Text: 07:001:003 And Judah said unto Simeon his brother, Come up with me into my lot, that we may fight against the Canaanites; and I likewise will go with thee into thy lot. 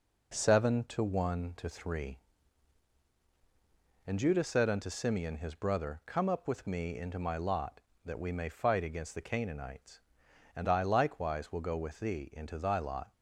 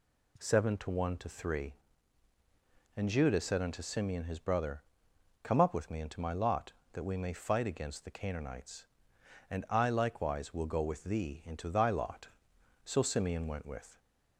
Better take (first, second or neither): first